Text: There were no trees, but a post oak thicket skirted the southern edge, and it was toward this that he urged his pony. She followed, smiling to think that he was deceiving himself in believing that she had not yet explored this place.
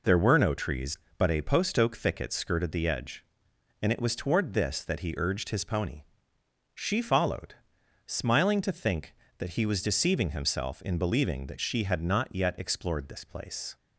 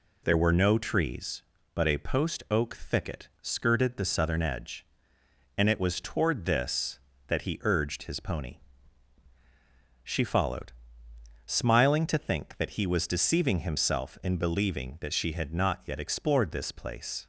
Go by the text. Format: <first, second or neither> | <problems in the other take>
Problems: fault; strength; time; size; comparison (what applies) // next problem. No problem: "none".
second | skips "southern"; at 2.8 s